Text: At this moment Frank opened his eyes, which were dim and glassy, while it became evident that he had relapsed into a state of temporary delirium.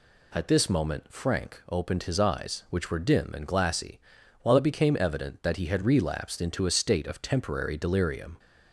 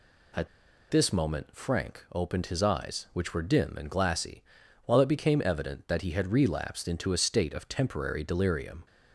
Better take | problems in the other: first | pauses between "At" and "this"; at 0.4 s; 0.43 s long

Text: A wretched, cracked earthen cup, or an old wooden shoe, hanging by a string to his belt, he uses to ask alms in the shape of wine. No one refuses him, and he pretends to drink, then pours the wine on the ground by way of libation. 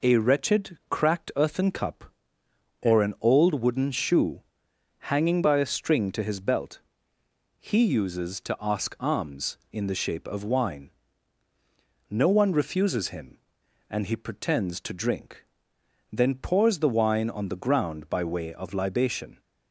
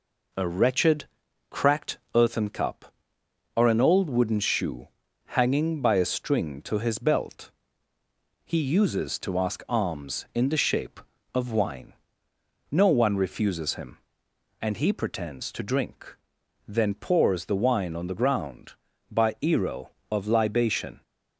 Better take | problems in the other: first | pauses between "cracked" and "earthen"; slight; at 1.9 s; 0.16 s long // says "ero" for "way"; at 19.4 s

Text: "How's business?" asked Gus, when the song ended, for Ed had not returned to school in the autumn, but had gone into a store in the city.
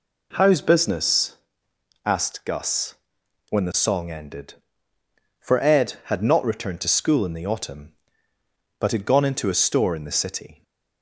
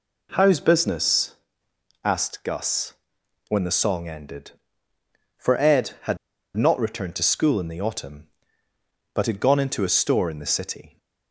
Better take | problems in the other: first | pauses between "had" and "not"; at 6.1 s; 0.40 s long

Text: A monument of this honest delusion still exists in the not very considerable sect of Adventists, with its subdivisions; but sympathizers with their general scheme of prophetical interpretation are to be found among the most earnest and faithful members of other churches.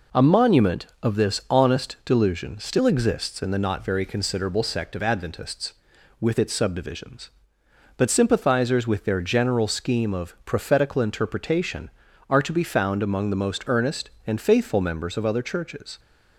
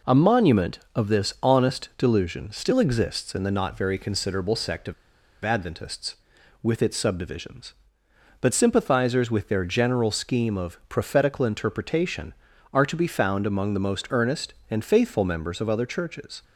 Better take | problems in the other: first | pauses between "of" and "Adventists"; noticeable; at 4.9 s; 0.50 s long

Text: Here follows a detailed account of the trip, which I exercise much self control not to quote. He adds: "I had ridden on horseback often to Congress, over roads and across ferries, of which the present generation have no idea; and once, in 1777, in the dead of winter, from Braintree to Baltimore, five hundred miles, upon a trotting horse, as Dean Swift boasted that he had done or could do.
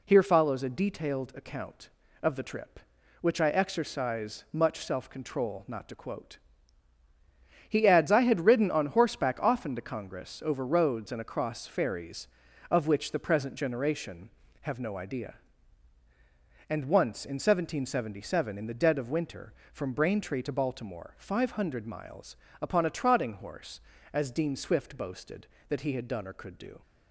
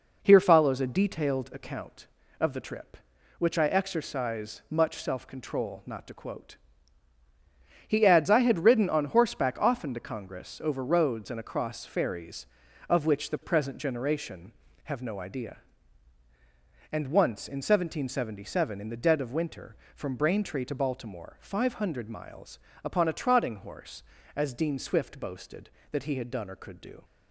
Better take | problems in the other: first | starts louder than the rest; noticeable; until 1.8 s; 4.5 dB

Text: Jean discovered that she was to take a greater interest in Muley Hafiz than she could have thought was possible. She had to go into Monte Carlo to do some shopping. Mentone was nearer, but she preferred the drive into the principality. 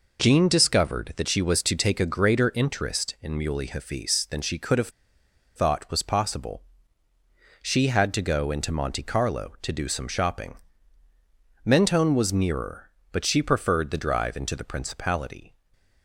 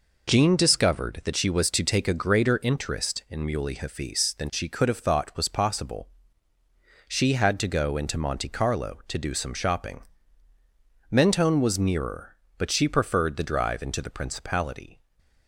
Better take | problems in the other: second | pauses between "have" and "thought"; noticeable; at 4.8 s; 0.66 s long // stays silent after the last word; slight; from 15.5 s on; 0.5 s long; slight in the second

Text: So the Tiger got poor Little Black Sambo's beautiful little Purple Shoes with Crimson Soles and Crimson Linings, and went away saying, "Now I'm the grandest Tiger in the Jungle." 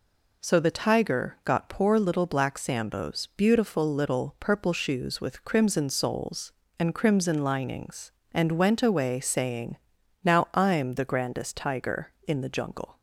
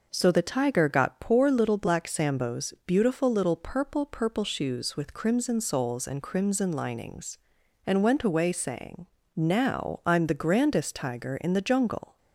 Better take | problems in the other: first | says "Purple" twice; at 4.0 s

